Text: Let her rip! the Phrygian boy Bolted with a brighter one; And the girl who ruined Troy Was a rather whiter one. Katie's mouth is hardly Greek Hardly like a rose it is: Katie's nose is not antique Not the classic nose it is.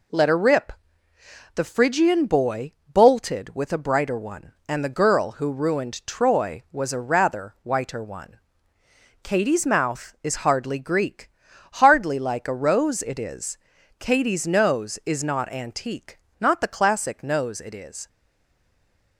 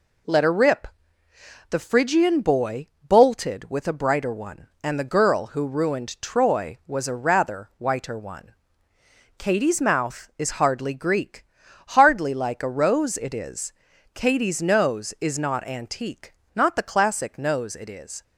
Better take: second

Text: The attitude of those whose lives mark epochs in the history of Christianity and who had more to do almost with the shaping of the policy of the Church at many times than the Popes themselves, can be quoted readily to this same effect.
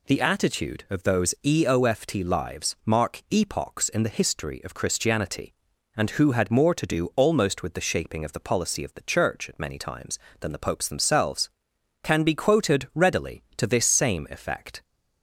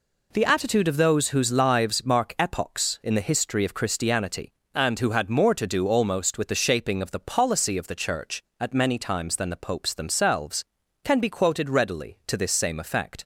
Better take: second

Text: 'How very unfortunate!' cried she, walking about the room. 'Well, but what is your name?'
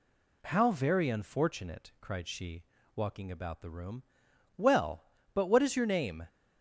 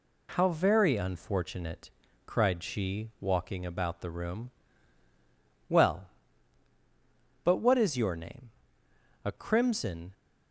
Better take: first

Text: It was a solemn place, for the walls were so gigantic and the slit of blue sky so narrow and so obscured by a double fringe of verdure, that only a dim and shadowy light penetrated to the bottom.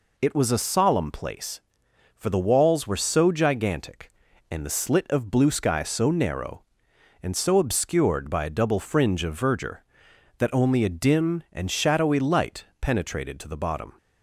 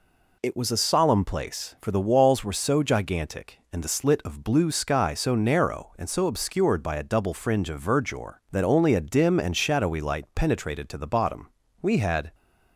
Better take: first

